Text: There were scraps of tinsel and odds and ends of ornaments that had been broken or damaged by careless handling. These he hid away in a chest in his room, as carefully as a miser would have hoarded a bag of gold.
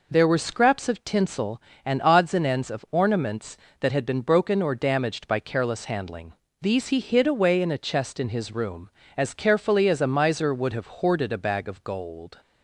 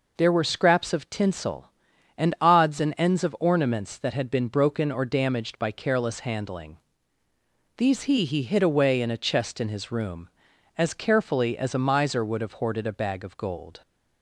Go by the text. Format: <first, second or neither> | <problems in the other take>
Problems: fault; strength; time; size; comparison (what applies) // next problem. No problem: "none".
first | says "he" twice; at 8.2 s